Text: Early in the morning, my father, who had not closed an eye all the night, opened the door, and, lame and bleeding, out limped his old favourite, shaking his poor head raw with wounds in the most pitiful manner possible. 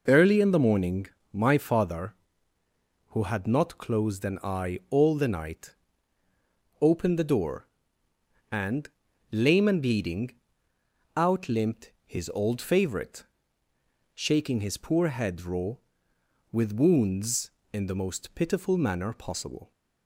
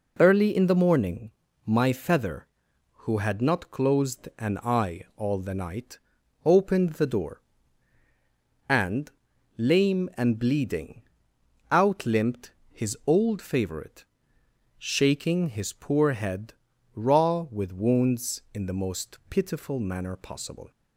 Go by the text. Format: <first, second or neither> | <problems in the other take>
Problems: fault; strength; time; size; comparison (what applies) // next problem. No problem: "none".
first | says "feather" for "father"; at 1.9 s // pauses between "limped" and "his"; slight; at 12.5 s; 0.20 s long // pauses between "head" and "raw"; at 16.5 s; 0.40 s long